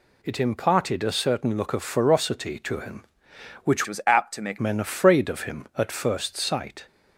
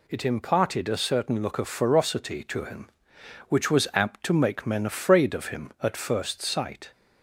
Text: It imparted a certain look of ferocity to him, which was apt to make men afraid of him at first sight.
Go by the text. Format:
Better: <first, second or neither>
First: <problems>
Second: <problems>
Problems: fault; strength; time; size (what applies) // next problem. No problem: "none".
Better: second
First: changes voice from "was" to "make"; from 3.8 to 4.5 s; 0.7 s long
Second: none